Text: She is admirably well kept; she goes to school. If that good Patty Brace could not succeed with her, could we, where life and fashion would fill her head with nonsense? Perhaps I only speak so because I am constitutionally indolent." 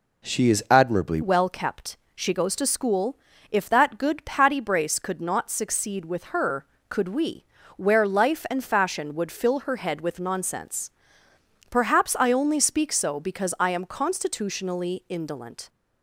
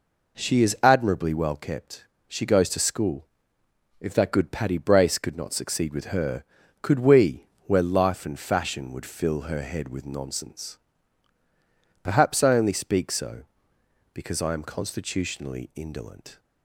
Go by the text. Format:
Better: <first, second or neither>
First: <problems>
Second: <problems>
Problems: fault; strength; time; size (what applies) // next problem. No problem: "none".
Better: second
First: changes voice at "well"; from 1.2 s on; 14.4 s long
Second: none